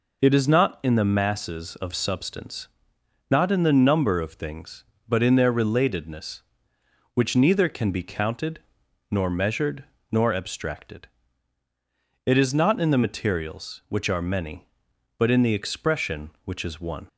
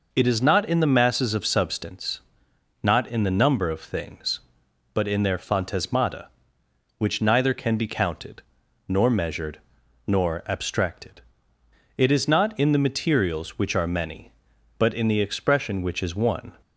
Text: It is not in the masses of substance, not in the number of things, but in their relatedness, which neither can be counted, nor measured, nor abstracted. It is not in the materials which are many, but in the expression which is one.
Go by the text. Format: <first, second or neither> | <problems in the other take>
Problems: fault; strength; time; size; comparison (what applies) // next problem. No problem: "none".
first | says "phantasmata" for "relatedness"; at 5.3 s